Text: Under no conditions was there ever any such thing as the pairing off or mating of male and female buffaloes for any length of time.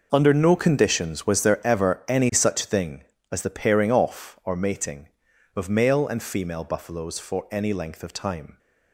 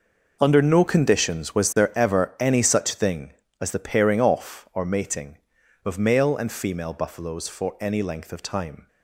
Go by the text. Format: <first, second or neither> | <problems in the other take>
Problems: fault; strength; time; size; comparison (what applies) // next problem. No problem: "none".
neither | none